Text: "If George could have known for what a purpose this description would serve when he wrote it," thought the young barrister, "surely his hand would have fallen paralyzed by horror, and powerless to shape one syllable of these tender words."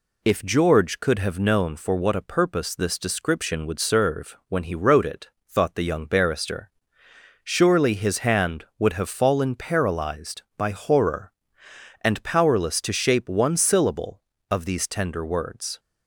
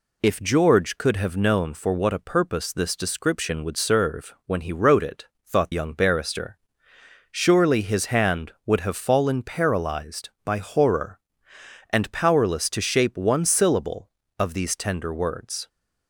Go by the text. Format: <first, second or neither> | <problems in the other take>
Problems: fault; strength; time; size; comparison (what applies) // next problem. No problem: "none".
first | skips "the"; at 5.7 s